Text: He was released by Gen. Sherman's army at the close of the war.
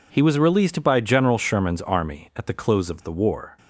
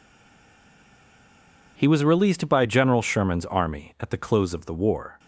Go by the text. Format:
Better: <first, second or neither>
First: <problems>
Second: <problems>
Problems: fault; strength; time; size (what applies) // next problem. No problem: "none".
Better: first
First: none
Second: stays silent before the first word; noticeable; until 1.7 s; 1.7 s long